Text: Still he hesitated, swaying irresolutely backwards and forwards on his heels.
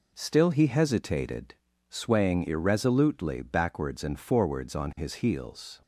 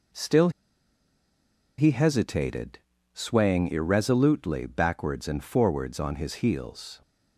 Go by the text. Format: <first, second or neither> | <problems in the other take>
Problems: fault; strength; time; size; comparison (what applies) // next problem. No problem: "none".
first | pauses between "Still" and "he"; strong; at 0.4 s; 1.2 s long